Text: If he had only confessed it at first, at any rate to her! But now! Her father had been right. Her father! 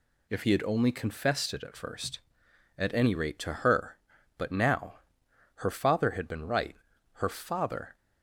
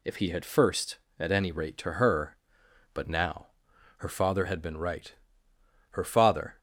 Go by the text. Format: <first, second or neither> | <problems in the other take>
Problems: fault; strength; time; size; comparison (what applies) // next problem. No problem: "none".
first | skips "only confessed it at"; at 0.4 s